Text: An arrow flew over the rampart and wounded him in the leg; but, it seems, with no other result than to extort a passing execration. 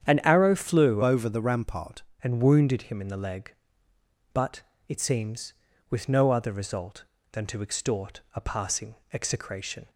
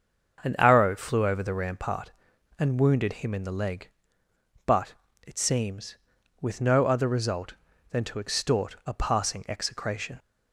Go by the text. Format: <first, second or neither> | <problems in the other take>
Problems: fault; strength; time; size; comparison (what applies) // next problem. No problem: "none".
second | starts louder than the rest; strong; until 1.1 s; 9 dB; also in the second // changes voice from "over" to "rampart"; from 1.0 to 2.0 s; 1.0 s long // pauses between "passing" and "execration"; slight; at 8.9 s; 0.18 s long